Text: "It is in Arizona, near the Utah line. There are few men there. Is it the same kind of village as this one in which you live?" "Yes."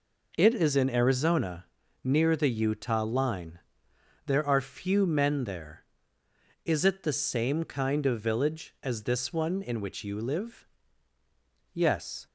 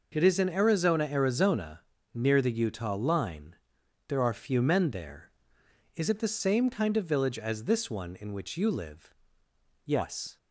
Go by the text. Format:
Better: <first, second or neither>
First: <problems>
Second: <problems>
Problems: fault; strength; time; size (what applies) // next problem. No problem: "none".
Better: first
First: none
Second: says "Arizona" twice; at 1.0 s